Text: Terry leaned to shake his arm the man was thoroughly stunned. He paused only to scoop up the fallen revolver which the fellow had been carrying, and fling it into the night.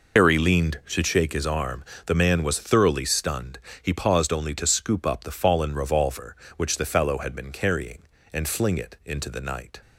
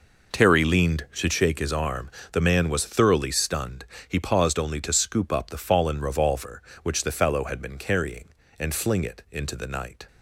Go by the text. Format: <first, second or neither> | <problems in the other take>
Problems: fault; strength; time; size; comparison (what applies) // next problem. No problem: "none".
second | loses the start of "Terry"; at 0.1 s; 115 ms // pauses between "arm" and "the"; slight; at 1.8 s; 0.24 s long; slight in the second